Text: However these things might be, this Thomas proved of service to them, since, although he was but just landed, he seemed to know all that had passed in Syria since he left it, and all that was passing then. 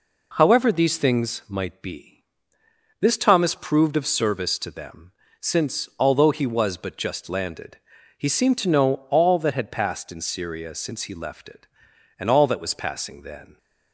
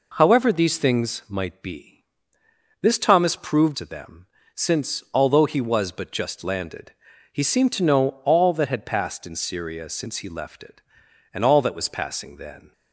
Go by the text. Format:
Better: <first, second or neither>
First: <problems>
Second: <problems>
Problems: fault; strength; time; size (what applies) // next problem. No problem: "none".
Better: first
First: none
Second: skips "of service"; at 3.7 s